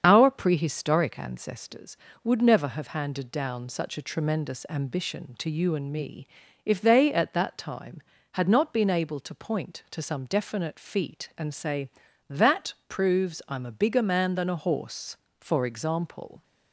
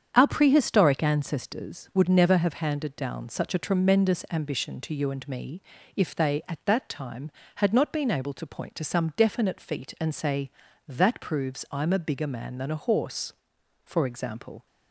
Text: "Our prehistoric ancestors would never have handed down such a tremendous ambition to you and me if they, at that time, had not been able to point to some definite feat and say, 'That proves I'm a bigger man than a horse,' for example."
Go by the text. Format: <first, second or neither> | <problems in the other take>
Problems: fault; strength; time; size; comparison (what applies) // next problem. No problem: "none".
second | loses the start of "Our"; at 0.0 s; 50 ms // starts louder than the rest; strong; until 1.0 s; 7.5 dB; strong in the second // pauses between "me" and "if"; at 6.2 s; 0.38 s long; slight in the second